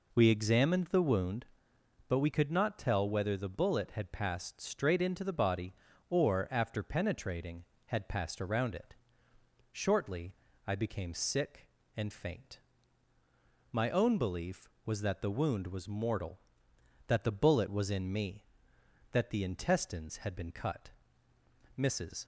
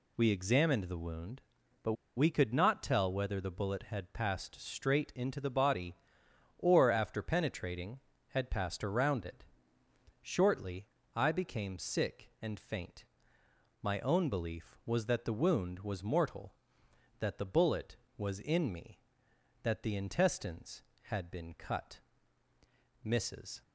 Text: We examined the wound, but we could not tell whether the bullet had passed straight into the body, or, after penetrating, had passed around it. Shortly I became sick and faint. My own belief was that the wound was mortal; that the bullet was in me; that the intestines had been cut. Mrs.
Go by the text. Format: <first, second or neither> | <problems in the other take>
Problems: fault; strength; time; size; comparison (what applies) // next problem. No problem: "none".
first | pauses between "but" and "we"; slight; at 1.9 s; 0.22 s long // pauses between "Shortly" and "I"; slight; at 10.8 s; 0.30 s long; slight in the first